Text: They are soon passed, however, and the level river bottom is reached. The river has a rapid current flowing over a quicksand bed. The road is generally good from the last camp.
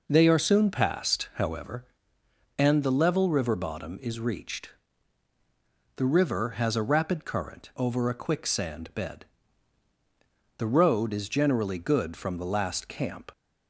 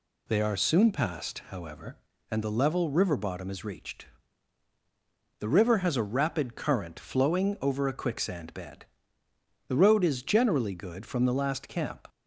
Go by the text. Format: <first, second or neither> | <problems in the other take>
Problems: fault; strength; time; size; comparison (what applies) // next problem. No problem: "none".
second | skips "flowing"; at 7.7 s